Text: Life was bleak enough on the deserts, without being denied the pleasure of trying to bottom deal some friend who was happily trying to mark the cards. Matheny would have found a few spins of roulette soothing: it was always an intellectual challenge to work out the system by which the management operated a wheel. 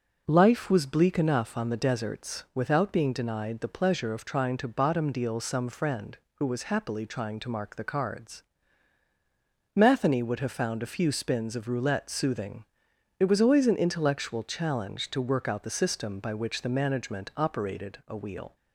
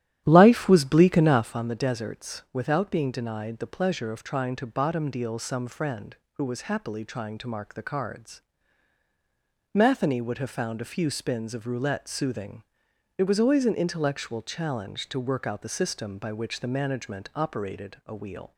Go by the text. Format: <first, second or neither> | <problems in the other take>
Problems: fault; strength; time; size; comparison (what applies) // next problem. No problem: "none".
first | starts louder than the rest; strong; until 1.7 s; 11 dB